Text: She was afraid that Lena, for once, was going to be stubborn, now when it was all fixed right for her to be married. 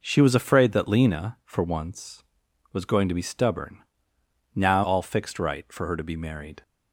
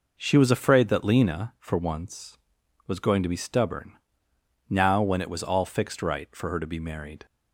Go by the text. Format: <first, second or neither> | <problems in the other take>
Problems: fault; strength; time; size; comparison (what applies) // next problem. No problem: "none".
second | skips "when it was"; at 4.8 s